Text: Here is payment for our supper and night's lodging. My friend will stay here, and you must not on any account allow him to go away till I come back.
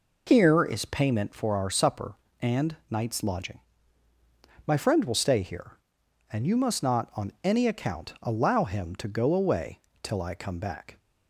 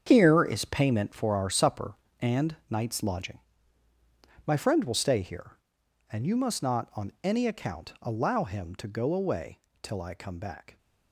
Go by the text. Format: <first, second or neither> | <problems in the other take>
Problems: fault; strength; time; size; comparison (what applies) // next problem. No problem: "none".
first | gets quieter; strong; throughout; 11.5 dB // pauses between "away" and "till"; slight; at 9.5 s; 0.22 s long; slight in the first